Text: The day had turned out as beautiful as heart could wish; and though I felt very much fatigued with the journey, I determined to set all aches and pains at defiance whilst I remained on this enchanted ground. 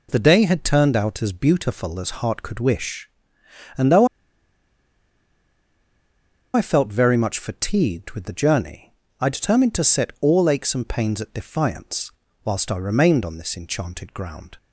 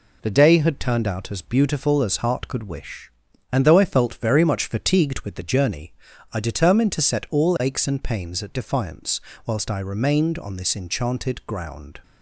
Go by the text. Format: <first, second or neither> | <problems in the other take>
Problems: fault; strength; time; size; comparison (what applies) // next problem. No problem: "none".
second | pauses between "though" and "I"; strong; at 4.0 s; 2.4 s long // pauses between "defiance" and "whilst"; slight; at 12.1 s; 0.34 s long; slight in the second